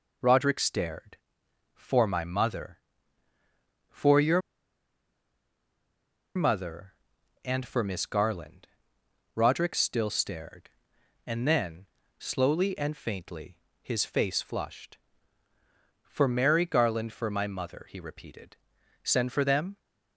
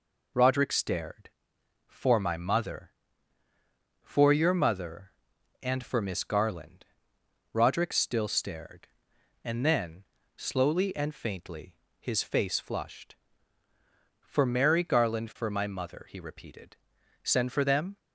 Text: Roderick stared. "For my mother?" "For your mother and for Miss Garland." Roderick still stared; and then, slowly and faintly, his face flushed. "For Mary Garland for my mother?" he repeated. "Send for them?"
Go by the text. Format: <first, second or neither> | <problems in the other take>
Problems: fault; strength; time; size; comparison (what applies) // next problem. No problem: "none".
second | pauses between "your" and "mother"; strong; at 4.4 s; 1.9 s long